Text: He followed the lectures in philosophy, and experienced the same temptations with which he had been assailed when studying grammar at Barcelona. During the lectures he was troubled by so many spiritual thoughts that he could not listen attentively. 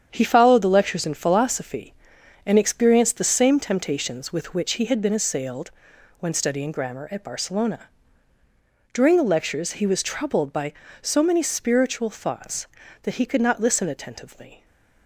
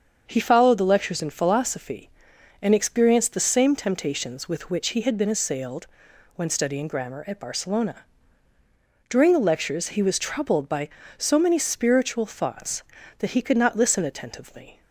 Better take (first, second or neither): second